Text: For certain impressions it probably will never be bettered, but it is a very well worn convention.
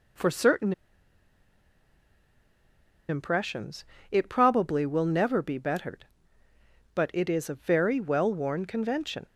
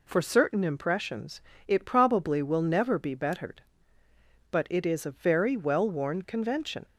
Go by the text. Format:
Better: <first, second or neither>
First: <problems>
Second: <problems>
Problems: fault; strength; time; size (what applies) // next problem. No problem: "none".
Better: second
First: pauses between "certain" and "impressions"; strong; at 0.7 s; 2.3 s long // pauses between "impressions" and "it"; slight; at 3.8 s; 0.26 s long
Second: pauses between "impressions" and "it"; slight; at 1.4 s; 0.26 s long